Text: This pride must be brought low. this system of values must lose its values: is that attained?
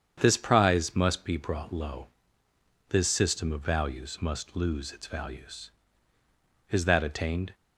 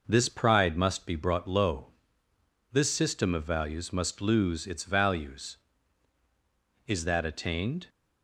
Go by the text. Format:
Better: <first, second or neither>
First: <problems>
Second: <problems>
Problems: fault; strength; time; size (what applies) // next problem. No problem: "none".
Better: second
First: starts louder than the rest; strong; until 1.2 s; 8 dB // says "prize" for "pride"; at 0.3 s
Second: none